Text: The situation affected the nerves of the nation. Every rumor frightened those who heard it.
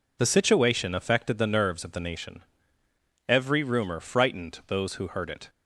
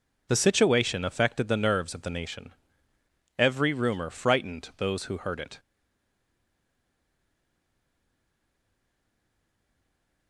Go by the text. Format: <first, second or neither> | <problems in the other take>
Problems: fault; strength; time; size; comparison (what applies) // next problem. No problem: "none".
first | stays silent after the last word; strong; from 5.5 s on; 4.7 s long